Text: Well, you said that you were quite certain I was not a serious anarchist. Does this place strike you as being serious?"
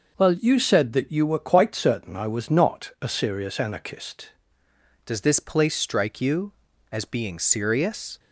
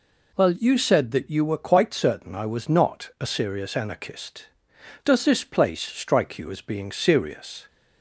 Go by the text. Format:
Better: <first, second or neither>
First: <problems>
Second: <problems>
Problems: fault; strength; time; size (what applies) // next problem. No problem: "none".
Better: second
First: changes voice at "Does"; from 5.0 s on; 3.1 s long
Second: none